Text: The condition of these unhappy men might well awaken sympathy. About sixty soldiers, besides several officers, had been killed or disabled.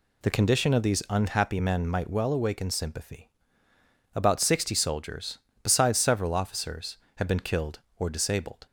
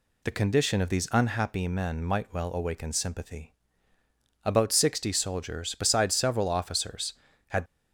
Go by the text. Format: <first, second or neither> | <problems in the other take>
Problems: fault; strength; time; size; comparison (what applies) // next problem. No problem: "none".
first | stops before "been killed or disabled"; at 7.6 s